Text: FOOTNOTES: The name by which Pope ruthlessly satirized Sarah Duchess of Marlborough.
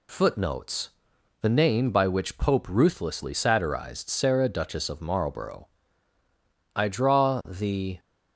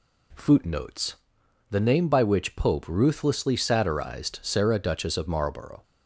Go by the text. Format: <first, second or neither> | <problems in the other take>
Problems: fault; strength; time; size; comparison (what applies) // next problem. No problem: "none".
second | goes on to say "I draw the"; noticeable; from 6.7 s on; 1.2 s long